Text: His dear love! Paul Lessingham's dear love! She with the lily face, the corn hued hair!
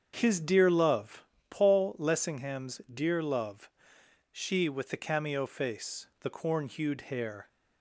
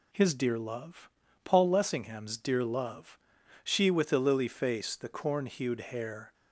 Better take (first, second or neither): second